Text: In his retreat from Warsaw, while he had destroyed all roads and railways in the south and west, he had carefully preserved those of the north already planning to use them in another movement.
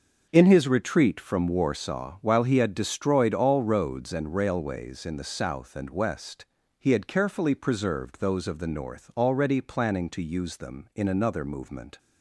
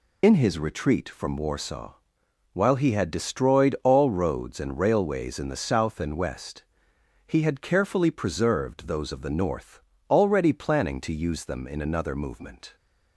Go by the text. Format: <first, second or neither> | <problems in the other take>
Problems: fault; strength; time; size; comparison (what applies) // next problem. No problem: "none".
first | loses the start of "In"; at 0.2 s; 35 ms // pauses between "north" and "already"; slight; at 9.8 s; 0.30 s long